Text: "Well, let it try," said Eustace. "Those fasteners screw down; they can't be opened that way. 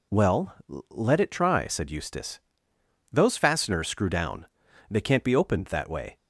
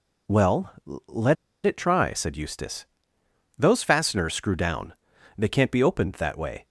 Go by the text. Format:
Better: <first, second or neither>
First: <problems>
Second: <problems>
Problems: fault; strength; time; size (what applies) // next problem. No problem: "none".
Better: first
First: none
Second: pauses between "let" and "it"; slight; at 1.3 s; 0.31 s long